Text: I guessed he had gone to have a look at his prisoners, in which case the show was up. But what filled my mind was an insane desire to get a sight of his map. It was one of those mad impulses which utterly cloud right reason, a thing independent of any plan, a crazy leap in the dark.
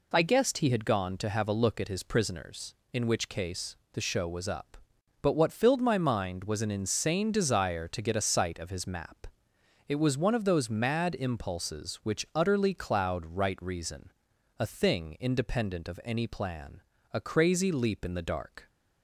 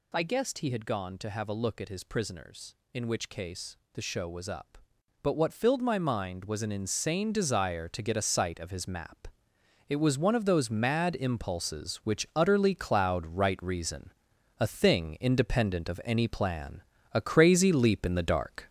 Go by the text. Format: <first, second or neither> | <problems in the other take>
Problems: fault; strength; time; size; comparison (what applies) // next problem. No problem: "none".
first | gets louder; noticeable; throughout; 4.5 dB // pauses between "case" and "the"; slight; at 3.7 s; 0.18 s long; slight in the first